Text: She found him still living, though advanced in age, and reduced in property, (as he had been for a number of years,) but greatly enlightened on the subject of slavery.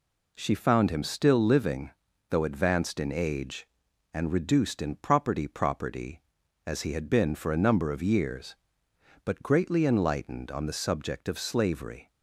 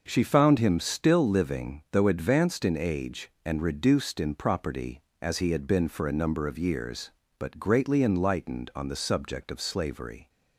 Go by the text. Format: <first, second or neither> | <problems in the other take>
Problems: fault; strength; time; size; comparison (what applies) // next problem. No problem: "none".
second | says "property" twice; at 5.4 s